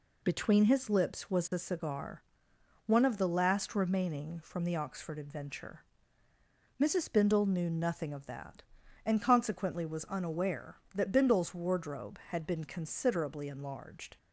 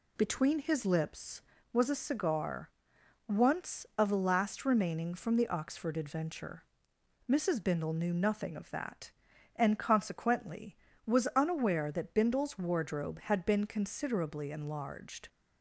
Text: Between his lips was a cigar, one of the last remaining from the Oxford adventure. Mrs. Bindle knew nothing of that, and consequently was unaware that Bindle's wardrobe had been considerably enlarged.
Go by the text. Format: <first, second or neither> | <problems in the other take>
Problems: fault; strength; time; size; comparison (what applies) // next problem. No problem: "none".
first | says "once" for "one"; at 3.2 s